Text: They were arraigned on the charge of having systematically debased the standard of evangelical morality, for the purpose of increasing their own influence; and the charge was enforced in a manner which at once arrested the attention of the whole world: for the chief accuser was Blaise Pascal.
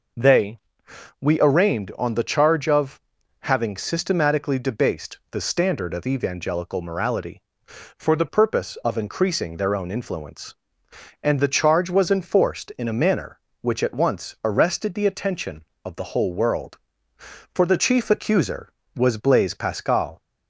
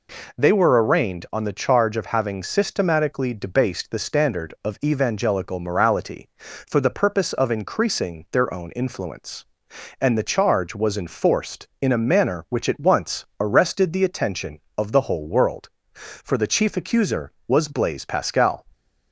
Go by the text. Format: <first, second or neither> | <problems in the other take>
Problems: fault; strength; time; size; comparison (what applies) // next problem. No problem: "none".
second | says "we" for "were"; at 1.1 s // pauses between "of" and "having"; at 2.9 s; 0.42 s long